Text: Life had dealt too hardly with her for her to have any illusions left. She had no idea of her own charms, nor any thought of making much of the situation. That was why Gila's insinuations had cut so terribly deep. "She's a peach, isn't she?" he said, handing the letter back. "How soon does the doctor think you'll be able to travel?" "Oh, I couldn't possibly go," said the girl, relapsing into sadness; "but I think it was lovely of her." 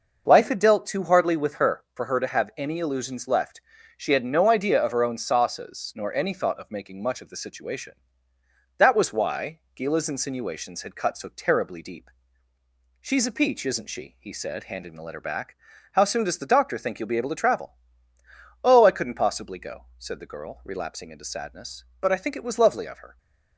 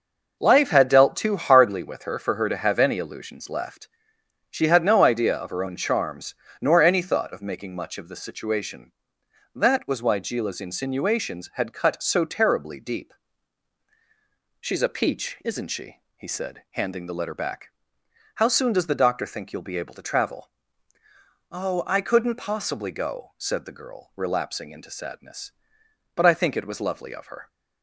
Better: second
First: says "sauces" for "charms"; at 5.1 s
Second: none

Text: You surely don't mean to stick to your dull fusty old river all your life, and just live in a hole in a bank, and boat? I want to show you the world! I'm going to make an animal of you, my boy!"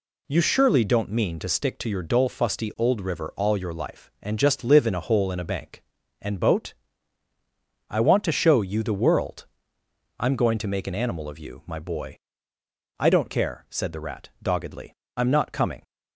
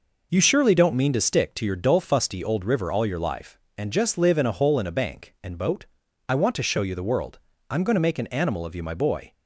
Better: second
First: goes on to say "I don't care said the Rat doggedly I'm not coming"; strong; from 12.9 s on; 2.8 s long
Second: none

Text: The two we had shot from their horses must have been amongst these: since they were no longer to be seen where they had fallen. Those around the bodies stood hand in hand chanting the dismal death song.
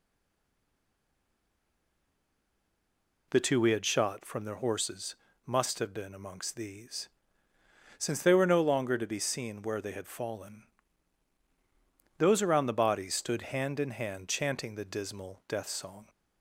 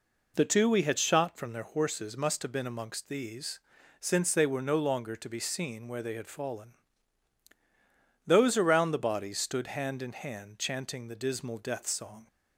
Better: second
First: stays silent before the first word; strong; until 3.3 s; 3.3 s long // pauses between "horses" and "must"; slight; at 5.1 s; 0.30 s long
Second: none

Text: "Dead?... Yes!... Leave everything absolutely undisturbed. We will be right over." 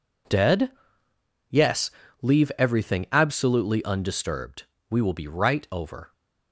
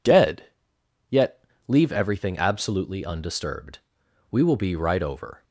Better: first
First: none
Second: says "Yet" for "Yes"; at 1.0 s

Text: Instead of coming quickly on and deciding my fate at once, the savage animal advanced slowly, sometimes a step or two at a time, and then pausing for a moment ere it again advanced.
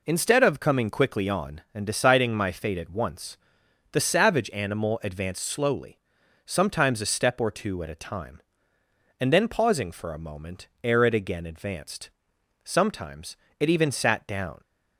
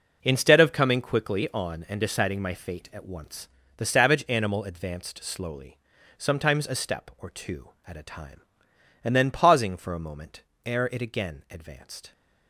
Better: second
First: pauses between "moment" and "ere"; slight; at 10.6 s; 0.16 s long // goes on to say "Sometimes it even sat down"; strong; from 12.6 s on; 1.9 s long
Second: pauses between "moment" and "ere"; slight; at 10.4 s; 0.24 s long

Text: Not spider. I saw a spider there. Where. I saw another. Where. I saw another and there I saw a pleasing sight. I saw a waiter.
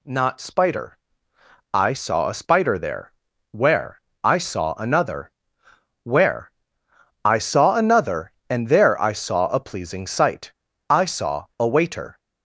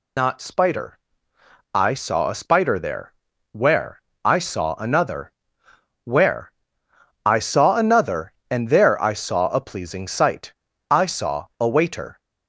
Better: first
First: none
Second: loses the start of "Not"; at 0.1 s; 135 ms

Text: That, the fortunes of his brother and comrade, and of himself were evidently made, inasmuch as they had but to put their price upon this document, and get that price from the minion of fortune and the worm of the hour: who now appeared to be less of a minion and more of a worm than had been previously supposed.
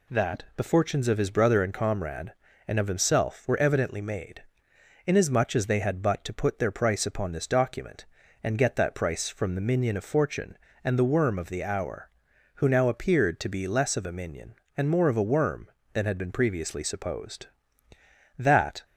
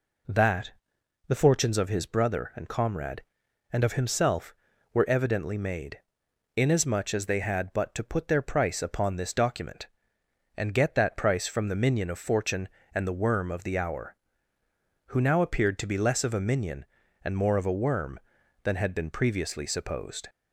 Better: second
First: goes on to say "That"; slight; from 18.3 s on; 0.48 s long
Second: none

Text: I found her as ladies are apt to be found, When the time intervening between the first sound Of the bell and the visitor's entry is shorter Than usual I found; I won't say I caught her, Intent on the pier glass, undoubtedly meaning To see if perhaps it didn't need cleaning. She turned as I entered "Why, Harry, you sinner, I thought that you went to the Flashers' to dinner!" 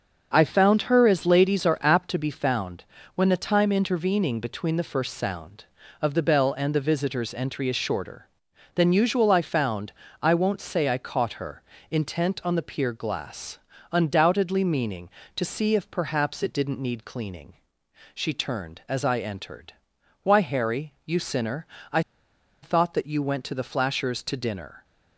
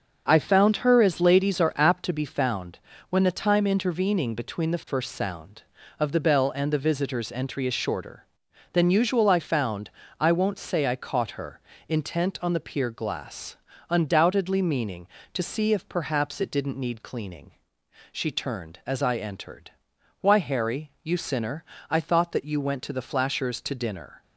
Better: second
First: starts louder than the rest; until 1.3 s; 6.5 dB // pauses between "entered" and "Why"; noticeable; at 19.7 s; 0.48 s long // pauses between "I" and "thought"; noticeable; at 22.0 s; 0.62 s long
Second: starts louder than the rest; until 1.2 s; 6.5 dB // pauses between "entered" and "Why"; noticeable; at 19.7 s; 0.48 s long

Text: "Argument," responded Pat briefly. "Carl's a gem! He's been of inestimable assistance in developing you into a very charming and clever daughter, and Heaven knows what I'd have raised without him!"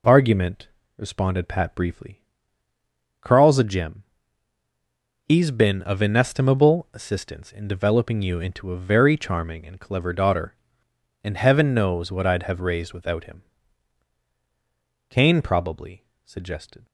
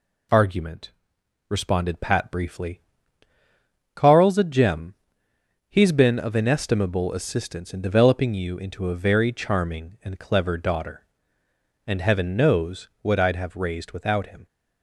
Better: second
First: goes on to say "Cain probably suggested"; strong; from 15.0 s on; 1.7 s long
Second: none

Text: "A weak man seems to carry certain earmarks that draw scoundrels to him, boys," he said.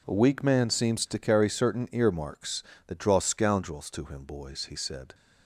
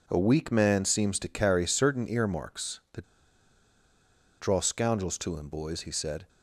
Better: first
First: none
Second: pauses between "that" and "draw"; strong; at 3.0 s; 1.3 s long

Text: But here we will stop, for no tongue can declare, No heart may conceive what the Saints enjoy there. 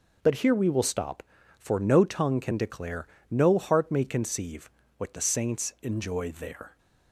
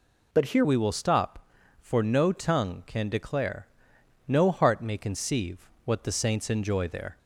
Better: first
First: pauses between "conceive" and "what"; slight; at 4.6 s; 0.28 s long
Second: changes voice at "we"; from 0.6 s on; 6.5 s long // pauses between "conceive" and "what"; slight; at 5.5 s; 0.26 s long

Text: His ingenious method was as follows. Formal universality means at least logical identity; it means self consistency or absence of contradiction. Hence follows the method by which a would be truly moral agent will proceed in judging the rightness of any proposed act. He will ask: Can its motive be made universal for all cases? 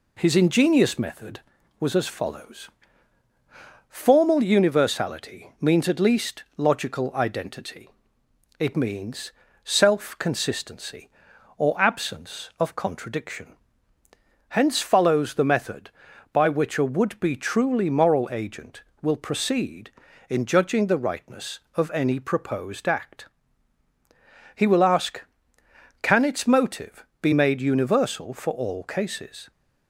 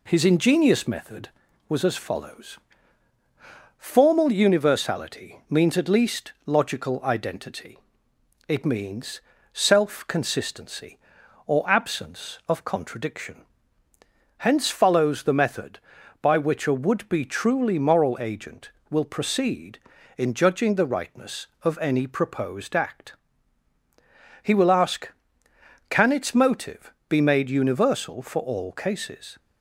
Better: neither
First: pauses between "least" and "logical"; slight; at 6.4 s; 0.16 s long // pauses between "means" and "self"; slight; at 9.3 s; 0.32 s long // pauses between "motive" and "be"; slight; at 27.0 s; 0.16 s long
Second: pauses between "least" and "logical"; slight; at 6.3 s; 0.16 s long // pauses between "means" and "self"; slight; at 9.2 s; 0.32 s long // pauses between "motive" and "be"; slight; at 26.9 s; 0.16 s long

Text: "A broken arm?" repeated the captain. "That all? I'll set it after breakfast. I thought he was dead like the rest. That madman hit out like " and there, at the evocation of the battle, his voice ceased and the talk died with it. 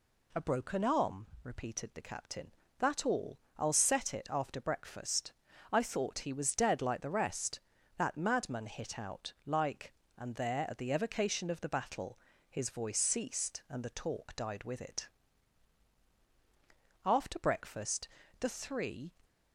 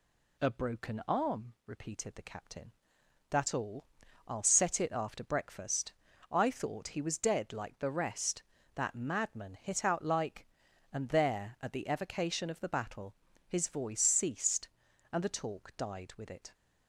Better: second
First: goes on to say "After breakfast the three"; strong; from 17.0 s on; 2.0 s long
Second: none

